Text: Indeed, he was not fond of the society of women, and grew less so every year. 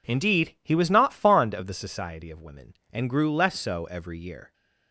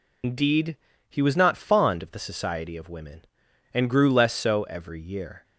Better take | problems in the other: first | loses the start of "Indeed"; at 0.2 s; 90 ms

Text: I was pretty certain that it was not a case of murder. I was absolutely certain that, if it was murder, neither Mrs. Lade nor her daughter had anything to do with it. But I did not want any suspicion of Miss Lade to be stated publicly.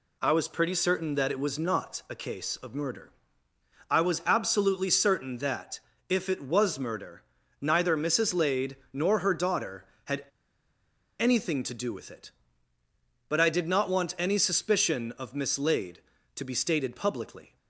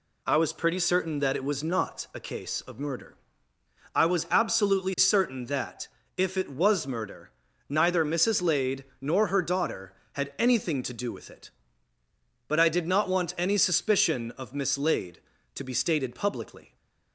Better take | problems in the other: second | pauses between "Lade" and "nor"; slight; at 8.7 s; 0.16 s long; slight in the second // pauses between "had" and "anything"; noticeable; at 10.2 s; 0.95 s long

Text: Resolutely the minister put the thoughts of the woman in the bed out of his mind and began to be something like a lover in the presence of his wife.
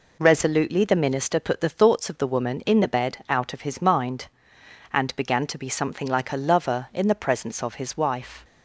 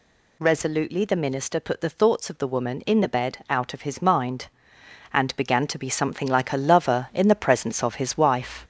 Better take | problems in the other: first | gets louder; noticeable; throughout; 4 dB

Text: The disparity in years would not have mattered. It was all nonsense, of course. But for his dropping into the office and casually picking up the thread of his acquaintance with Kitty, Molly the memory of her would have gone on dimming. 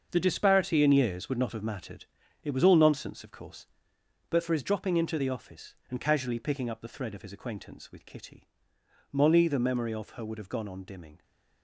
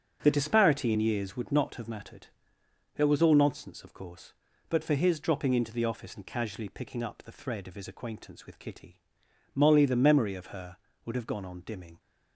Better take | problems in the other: second | gets quieter; strong; throughout; 11 dB // starts louder than the rest; until 1.1 s; 6.5 dB; also in the second

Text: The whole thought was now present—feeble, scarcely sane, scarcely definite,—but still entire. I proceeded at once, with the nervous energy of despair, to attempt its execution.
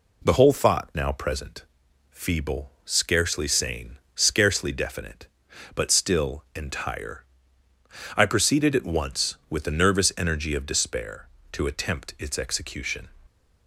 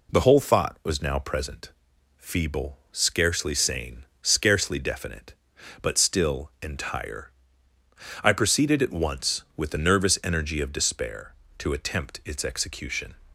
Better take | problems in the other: second | skips "was"; at 0.9 s

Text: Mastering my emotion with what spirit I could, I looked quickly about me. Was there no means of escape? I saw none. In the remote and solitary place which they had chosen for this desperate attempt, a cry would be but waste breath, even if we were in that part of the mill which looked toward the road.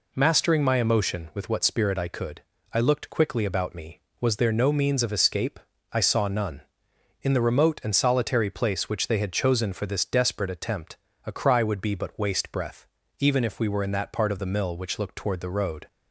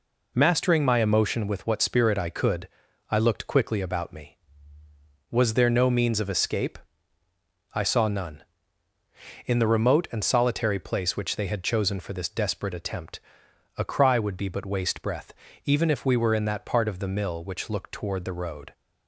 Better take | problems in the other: neither | none

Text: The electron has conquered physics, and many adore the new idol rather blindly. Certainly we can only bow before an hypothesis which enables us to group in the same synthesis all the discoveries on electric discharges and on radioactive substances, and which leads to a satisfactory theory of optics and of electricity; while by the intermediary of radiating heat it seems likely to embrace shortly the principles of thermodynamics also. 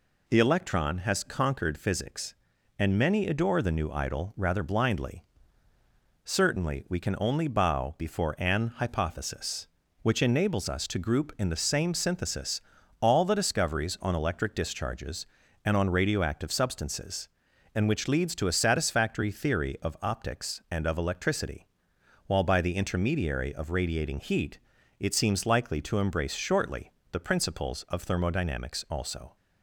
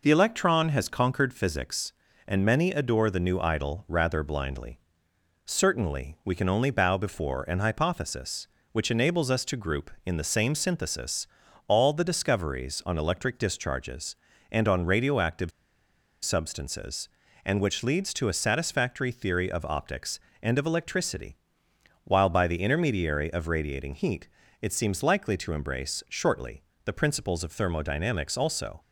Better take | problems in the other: first | pauses between "synthesis" and "all"; at 11.2 s; 0.42 s long; also in the first // pauses between "radioactive" and "substances"; noticeable; at 15.5 s; 0.74 s long // pauses between "heat" and "it"; slight; at 24.2 s; 0.34 s long; also in the first // pauses between "shortly" and "the"; slight; at 26.6 s; 0.20 s long; slight in the first

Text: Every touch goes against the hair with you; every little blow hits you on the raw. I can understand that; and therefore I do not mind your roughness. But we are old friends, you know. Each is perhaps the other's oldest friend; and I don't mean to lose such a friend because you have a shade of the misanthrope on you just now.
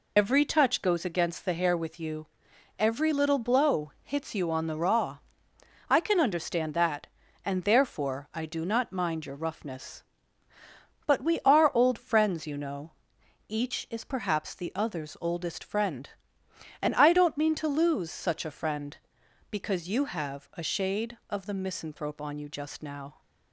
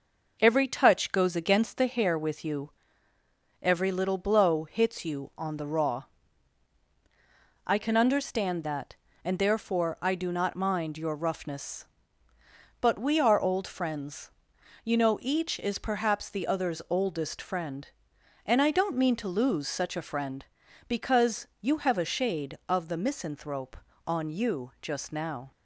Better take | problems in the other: second | loses the start of "Every"; at 0.1 s; 95 ms

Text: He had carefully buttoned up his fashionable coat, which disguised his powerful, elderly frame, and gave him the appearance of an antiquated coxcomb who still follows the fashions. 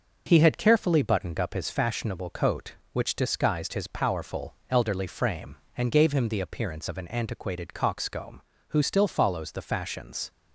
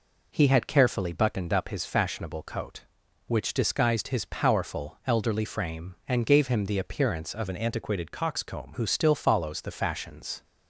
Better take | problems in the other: first | changes voice from "an" to "coxcomb"; from 7.4 to 8.7 s; 1.3 s long

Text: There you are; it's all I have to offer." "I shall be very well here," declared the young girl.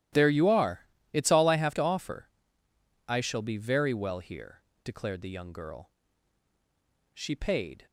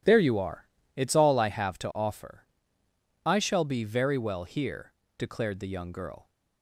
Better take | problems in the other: second | starts louder than the rest; strong; until 1.4 s; 13 dB // goes on to say "She paid"; noticeable; from 7.1 s on; 0.72 s long

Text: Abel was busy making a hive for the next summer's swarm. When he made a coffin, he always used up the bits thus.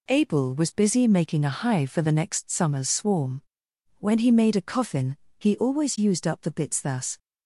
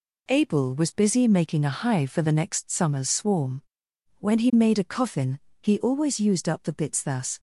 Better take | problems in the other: neither | none

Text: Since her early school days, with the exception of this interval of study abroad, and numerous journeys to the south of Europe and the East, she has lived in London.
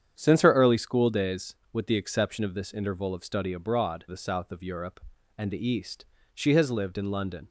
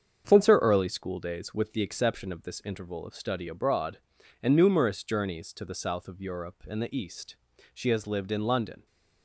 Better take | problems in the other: second | starts louder than the rest; strong; until 1.1 s; 8.5 dB; strong in the second // skips "and numerous journeys to"; at 4.0 s

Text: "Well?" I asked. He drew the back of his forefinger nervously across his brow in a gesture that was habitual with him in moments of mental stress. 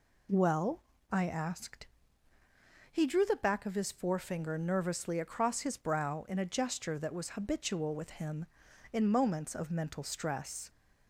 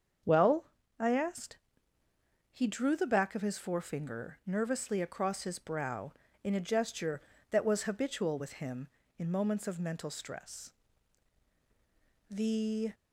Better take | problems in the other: first | starts louder than the rest; until 1.5 s; 7 dB // goes on to say "The"; noticeable; from 12.2 s on; 0.64 s long

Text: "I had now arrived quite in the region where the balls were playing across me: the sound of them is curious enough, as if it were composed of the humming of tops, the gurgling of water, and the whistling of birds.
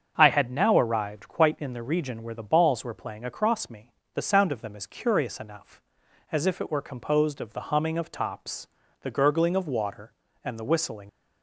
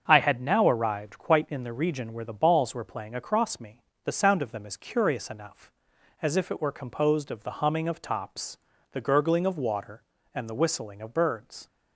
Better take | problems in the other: second | starts louder than the rest; strong; until 1.1 s; 7 dB; also in the second // stops before "of birds"; at 11.0 s

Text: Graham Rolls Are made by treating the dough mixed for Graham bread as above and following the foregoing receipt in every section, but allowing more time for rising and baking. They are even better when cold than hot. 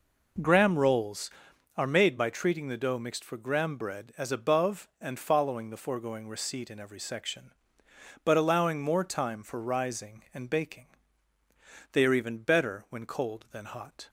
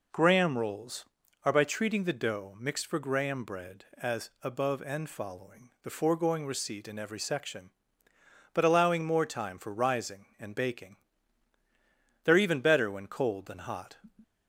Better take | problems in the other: first | skips "made"; at 1.5 s

